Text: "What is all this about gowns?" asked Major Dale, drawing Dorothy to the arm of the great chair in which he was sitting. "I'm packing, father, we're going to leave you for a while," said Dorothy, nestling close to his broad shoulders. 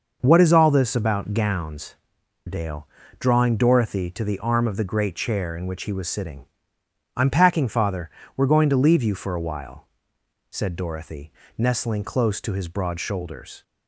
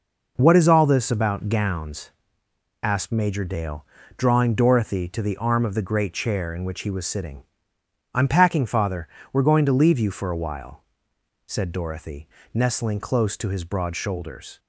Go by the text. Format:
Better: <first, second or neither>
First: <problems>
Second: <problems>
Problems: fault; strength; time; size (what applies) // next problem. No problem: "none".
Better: second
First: skips "asked Major"; at 2.2 s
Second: none